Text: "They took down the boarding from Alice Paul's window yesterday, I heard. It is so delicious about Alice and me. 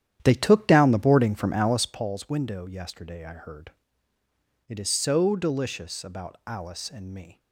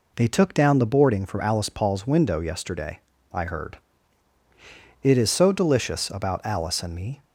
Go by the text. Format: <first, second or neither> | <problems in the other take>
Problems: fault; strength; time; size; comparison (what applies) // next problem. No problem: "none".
second | starts louder than the rest; strong; until 2.1 s; 10.5 dB